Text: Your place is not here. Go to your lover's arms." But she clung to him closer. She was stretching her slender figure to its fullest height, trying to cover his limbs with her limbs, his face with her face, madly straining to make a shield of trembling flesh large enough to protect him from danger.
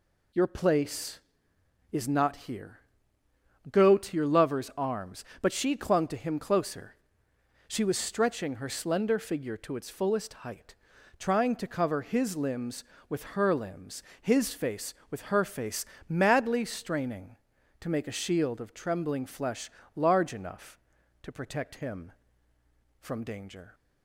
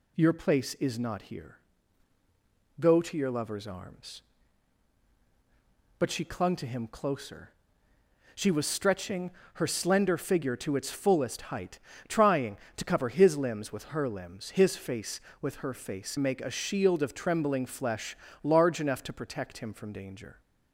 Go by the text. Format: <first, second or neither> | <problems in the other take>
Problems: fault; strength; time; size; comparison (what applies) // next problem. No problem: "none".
first | pauses between "stretching" and "her"; slight; at 9.3 s; 0.24 s long // skips "madly straining to"; at 16.1 s // pauses between "flesh" and "large"; slight; at 18.1 s; 0.26 s long; slight in the first